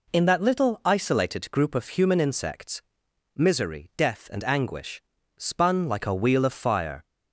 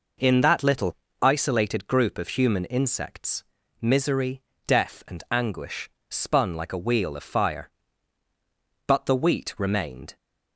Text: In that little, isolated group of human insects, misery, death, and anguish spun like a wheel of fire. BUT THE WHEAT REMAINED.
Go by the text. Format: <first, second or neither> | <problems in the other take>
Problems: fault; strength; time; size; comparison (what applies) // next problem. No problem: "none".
second | pauses between "anguish" and "spun"; slight; at 5.0 s; 0.34 s long; slight in the second // stops before "BUT THE WHEAT REMAINED"; at 7.0 s